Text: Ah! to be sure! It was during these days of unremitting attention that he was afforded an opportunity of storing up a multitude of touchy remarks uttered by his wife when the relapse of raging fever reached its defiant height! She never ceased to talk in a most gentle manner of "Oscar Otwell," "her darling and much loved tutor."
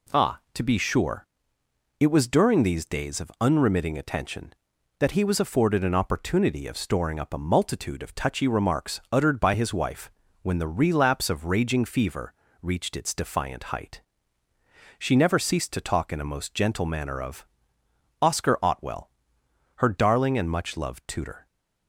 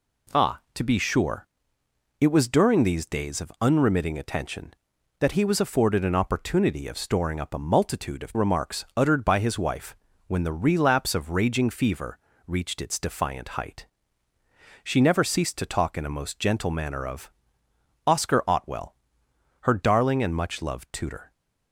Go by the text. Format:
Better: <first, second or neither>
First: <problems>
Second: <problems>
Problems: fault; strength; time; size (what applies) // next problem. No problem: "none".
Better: first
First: pauses between "wife" and "when"; slight; at 10.0 s; 0.34 s long // pauses between "fever" and "reached"; slight; at 12.3 s; 0.28 s long // pauses between "of" and "Oscar"; noticeable; at 17.4 s; 0.76 s long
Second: skips "touchy"; at 8.3 s // pauses between "wife" and "when"; slight; at 9.9 s; 0.34 s long // pauses between "fever" and "reached"; slight; at 12.1 s; 0.28 s long // pauses between "of" and "Oscar"; noticeable; at 17.3 s; 0.76 s long